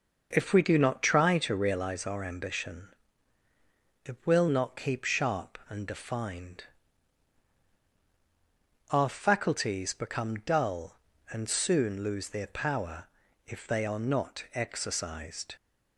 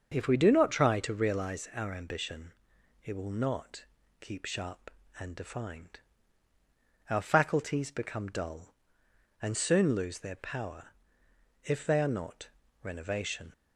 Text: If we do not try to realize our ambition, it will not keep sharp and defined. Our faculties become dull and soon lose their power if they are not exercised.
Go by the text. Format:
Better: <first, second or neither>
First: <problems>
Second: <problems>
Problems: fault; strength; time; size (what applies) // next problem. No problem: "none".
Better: first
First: starts louder than the rest; noticeable; until 1.3 s; 6 dB // pauses between "power" and "if"; at 13.0 s; 0.42 s long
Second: starts louder than the rest; until 1.1 s; 6.5 dB // pauses between "not" and "keep"; slight; at 3.8 s; 0.36 s long // pauses between "power" and "if"; noticeable; at 10.8 s; 0.76 s long // says "renovation" for "exercised"; at 12.8 s